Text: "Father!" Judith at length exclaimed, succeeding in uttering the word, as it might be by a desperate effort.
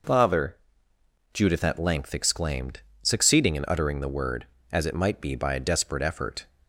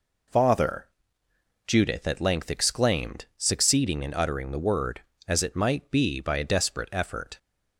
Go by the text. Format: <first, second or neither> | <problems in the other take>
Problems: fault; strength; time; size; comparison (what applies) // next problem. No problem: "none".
neither | none